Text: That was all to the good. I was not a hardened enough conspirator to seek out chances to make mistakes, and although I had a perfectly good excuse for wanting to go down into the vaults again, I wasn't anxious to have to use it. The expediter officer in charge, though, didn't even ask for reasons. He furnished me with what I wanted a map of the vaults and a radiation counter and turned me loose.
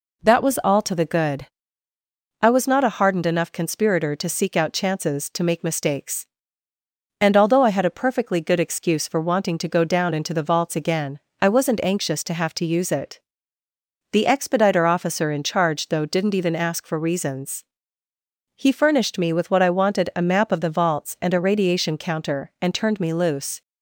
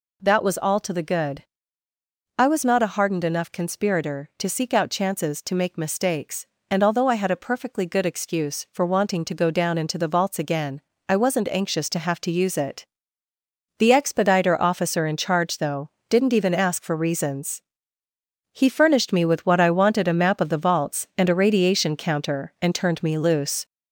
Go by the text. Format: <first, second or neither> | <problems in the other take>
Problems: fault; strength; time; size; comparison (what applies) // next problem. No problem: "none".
first | gets louder; throughout; 4 dB